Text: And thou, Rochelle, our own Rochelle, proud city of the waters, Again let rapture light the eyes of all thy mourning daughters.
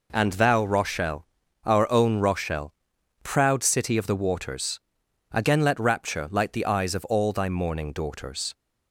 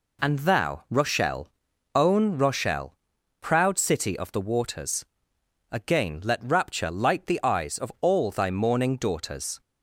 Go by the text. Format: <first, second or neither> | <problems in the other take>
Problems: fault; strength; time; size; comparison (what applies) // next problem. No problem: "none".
first | skips "our"; at 1.7 s